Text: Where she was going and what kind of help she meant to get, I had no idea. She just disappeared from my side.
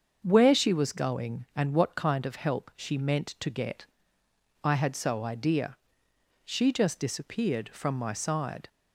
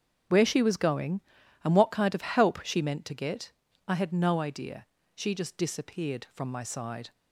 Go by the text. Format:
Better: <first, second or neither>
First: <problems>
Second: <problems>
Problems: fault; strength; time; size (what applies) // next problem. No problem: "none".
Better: second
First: starts louder than the rest; until 1.2 s; 7 dB // says "so" for "no"; at 4.9 s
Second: starts louder than the rest; strong; until 1.7 s; 7.5 dB